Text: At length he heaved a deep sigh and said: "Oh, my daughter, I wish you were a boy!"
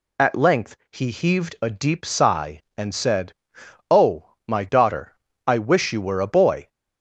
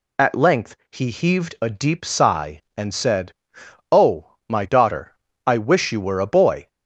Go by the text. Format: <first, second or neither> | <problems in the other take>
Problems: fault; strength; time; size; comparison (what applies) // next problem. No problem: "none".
neither | pauses between "length" and "he"; slight; the same in both